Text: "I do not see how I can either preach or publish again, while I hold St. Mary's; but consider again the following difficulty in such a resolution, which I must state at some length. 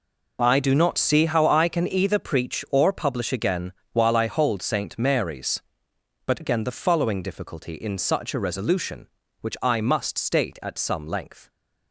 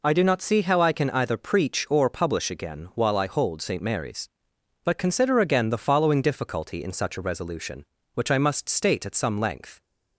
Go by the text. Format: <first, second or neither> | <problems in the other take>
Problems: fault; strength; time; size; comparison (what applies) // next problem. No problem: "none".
second | skips "consider"; at 6.4 s